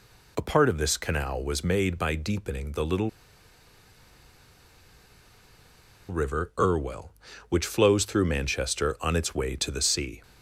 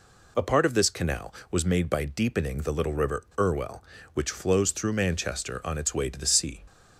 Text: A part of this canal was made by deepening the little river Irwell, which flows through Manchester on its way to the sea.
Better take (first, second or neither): second